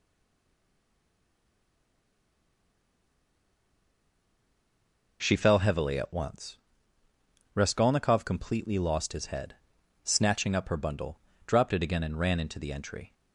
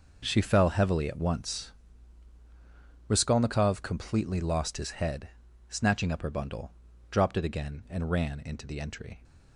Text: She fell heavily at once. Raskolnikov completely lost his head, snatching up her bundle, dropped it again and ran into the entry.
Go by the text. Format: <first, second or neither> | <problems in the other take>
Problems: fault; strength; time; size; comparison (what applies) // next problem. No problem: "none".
second | stays silent before the first word; strong; until 5.2 s; 5.2 s long